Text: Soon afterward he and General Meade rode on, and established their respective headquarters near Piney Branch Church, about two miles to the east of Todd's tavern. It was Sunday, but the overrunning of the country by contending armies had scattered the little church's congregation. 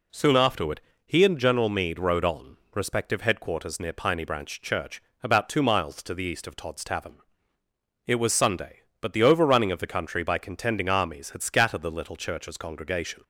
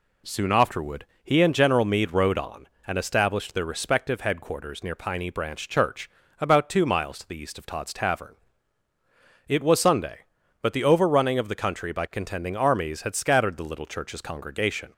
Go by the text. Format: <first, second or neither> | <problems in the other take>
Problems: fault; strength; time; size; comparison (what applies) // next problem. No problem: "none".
second | pauses between "afterward" and "he"; slight; at 0.7 s; 0.26 s long; slight in the second // skips "and established their"; at 2.6 s